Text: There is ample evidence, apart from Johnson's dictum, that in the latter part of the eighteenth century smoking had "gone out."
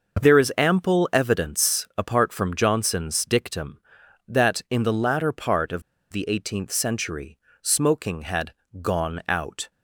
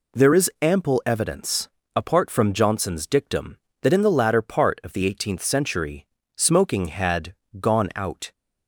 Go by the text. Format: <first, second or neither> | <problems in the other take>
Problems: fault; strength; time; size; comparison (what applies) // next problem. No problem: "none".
second | starts louder than the rest; noticeable; until 1.3 s; 6 dB // pauses between "of" and "the"; slight; at 5.8 s; 0.29 s long // pauses between "century" and "smoking"; slight; at 7.3 s; 0.26 s long; slight in the second // pauses between "had" and "gone"; slight; at 8.5 s; 0.28 s long; slight in the second